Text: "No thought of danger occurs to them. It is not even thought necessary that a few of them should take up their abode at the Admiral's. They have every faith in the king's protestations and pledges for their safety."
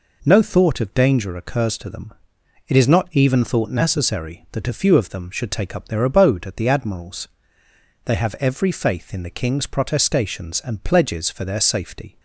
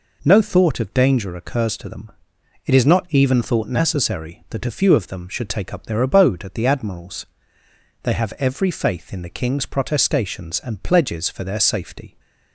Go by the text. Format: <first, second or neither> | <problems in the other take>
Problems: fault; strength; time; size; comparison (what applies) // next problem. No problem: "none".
neither | none